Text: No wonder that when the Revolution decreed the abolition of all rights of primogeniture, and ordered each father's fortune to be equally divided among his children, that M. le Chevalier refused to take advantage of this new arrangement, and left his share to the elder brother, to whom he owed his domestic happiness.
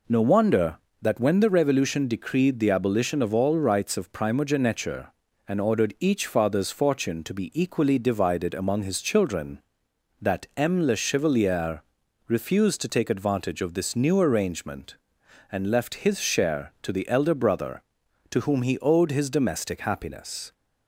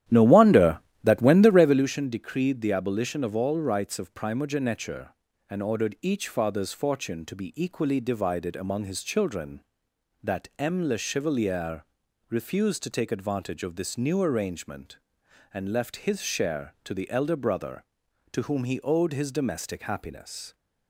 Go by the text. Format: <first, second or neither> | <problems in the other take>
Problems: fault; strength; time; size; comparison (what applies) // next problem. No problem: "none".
first | starts louder than the rest; strong; until 1.9 s; 12 dB // pauses between "Chevalier" and "refused"; at 11.8 s; 0.44 s long; also in the first